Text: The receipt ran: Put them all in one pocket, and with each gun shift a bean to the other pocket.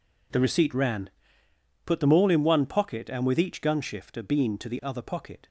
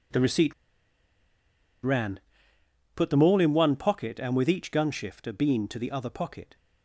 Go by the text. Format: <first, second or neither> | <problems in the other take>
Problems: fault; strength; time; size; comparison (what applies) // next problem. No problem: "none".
first | pauses between "receipt" and "ran"; strong; at 0.5 s; 1.2 s long